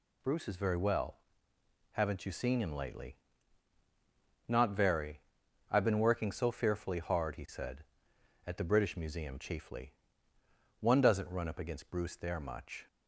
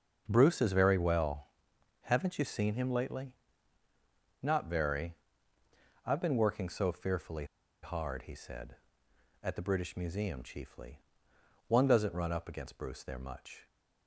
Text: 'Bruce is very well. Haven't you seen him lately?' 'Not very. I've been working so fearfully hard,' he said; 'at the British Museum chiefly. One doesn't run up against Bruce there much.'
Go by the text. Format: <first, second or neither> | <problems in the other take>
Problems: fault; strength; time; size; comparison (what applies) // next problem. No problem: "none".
first | starts louder than the rest; until 1.2 s; 6.5 dB // pauses between "fearfully" and "hard"; at 7.4 s; 0.38 s long